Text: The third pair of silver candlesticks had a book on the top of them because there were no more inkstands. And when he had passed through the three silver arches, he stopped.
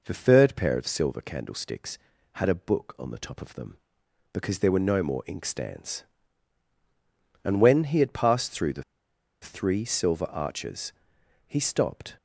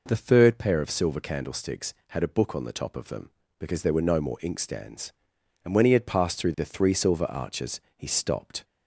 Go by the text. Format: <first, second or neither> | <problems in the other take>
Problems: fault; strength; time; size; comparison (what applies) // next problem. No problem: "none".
second | pauses between "the" and "three"; noticeable; at 8.8 s; 0.59 s long